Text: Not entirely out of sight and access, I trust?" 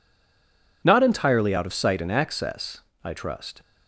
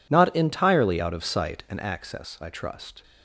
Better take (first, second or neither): second